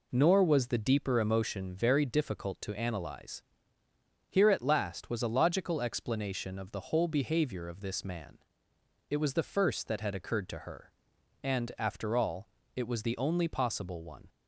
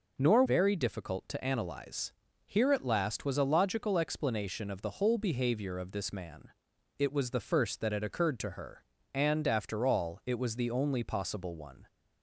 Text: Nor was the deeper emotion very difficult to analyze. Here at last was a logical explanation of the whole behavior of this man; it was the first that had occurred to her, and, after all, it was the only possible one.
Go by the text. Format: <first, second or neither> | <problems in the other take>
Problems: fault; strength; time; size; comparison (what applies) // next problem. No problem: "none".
first | skips "was the deeper emotion"; at 0.4 s